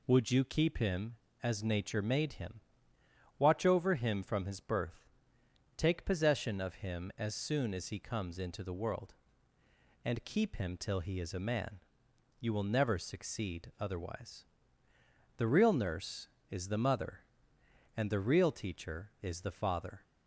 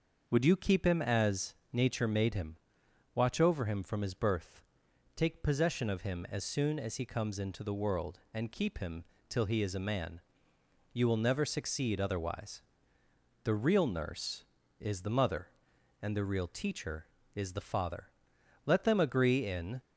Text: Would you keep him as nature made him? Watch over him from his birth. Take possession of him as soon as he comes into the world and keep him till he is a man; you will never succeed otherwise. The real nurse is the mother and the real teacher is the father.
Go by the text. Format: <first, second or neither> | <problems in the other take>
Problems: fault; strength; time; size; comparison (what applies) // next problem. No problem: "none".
first | starts louder than the rest; noticeable; until 1.3 s; 6 dB // pauses between "as" and "nature"; slight; at 1.5 s; 0.18 s long // pauses between "him" and "till"; slight; at 9.0 s; 0.24 s long // goes on to say "Let them agree in"; noticeable; from 18.6 s on; 1.1 s long